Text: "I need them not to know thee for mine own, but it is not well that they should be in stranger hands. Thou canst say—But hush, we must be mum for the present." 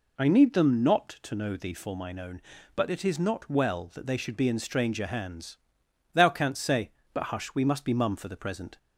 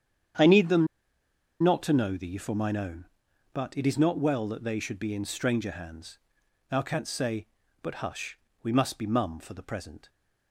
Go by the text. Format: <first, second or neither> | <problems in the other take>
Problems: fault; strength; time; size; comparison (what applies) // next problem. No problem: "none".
first | starts louder than the rest; strong; until 2.1 s; 9 dB // pauses between "them" and "not"; noticeable; at 0.8 s; 0.76 s long